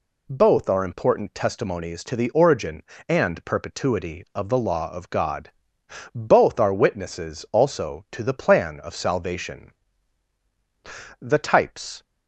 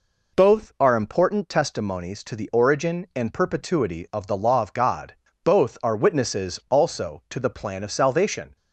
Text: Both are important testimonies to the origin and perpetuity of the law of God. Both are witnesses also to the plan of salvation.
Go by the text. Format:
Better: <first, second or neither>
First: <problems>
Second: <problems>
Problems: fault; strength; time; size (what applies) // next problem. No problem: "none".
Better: second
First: goes on to say "The types"; noticeable; from 11.2 s on; 0.82 s long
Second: none